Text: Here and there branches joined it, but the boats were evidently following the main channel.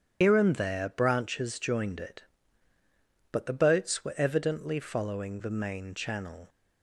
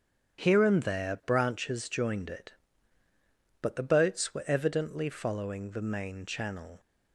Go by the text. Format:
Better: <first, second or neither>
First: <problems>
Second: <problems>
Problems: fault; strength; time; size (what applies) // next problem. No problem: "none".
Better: second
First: loses the start of "Here"; at 0.2 s; 95 ms // starts louder than the rest; strong; until 1.2 s; 9.5 dB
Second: starts louder than the rest; strong; until 1.4 s; 8.5 dB